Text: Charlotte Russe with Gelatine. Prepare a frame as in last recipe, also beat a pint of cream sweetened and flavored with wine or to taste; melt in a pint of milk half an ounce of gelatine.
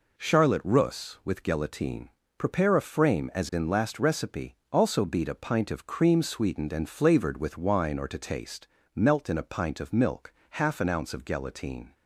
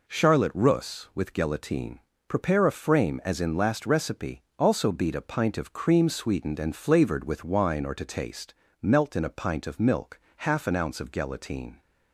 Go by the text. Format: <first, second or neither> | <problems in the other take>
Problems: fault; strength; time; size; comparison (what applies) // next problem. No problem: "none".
neither | pauses between "milk" and "half"; slight; the same in both